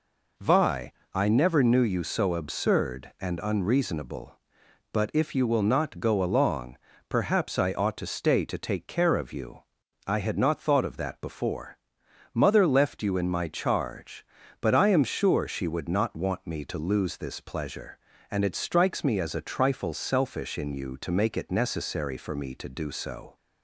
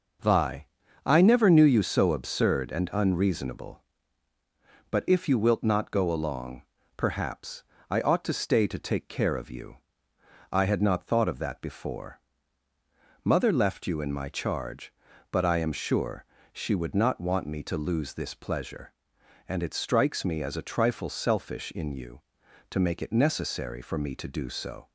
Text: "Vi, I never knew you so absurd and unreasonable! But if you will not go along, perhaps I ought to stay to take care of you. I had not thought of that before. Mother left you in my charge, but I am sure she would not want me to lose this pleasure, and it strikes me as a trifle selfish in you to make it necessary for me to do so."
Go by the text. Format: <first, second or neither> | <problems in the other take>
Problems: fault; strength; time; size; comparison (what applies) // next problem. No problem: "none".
first | says "wilt" for "will"; at 5.3 s // pauses between "perhaps" and "I"; slight; at 7.6 s; 0.26 s long // pauses between "sure" and "she"; slight; at 16.2 s; 0.28 s long